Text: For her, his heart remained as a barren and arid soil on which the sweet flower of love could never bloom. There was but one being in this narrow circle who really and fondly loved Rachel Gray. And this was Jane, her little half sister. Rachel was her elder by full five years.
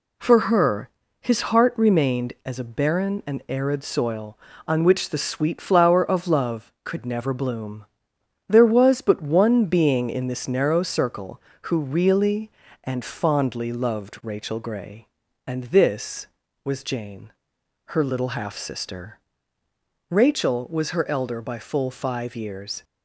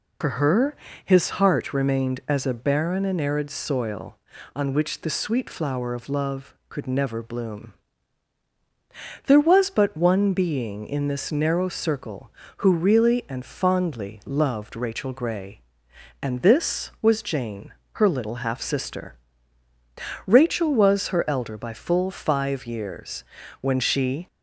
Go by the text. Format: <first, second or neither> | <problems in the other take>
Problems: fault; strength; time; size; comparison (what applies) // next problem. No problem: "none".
first | goes on to say "When she"; noticeable; from 23.6 s on; 0.66 s long